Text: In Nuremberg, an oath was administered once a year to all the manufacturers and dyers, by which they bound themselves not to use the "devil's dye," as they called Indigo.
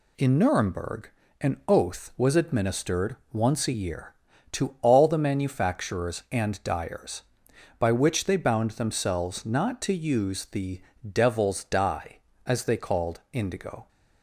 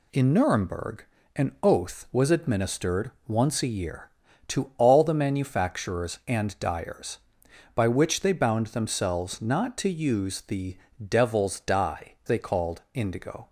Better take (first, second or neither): first